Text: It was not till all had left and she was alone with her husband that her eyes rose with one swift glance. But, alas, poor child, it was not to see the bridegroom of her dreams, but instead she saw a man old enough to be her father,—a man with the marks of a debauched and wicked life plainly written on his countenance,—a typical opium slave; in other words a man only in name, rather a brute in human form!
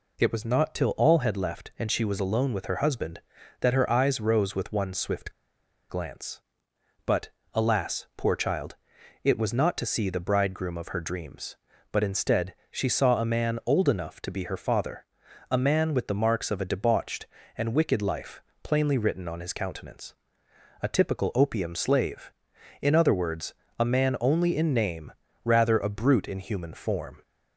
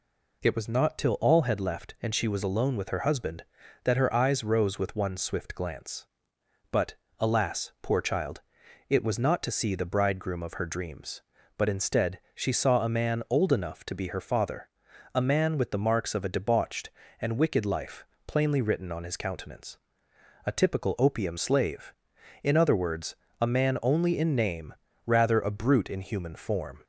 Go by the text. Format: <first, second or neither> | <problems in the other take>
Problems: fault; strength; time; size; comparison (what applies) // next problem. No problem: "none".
second | pauses between "swift" and "glance"; noticeable; at 5.2 s; 0.59 s long // pauses between "instead" and "she"; slight; at 12.5 s; 0.18 s long; slight in the second // pauses between "life" and "plainly"; slight; at 18.4 s; 0.22 s long; slight in the second // pauses between "words" and "a"; slight; at 23.5 s; 0.24 s long; slight in the second